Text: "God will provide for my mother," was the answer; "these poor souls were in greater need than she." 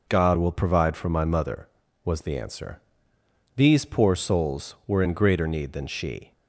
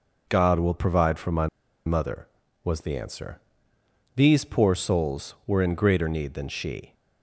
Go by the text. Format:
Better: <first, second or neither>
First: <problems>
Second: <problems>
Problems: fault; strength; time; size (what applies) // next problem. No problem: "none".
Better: first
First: none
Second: pauses between "my" and "mother"; at 1.4 s; 0.39 s long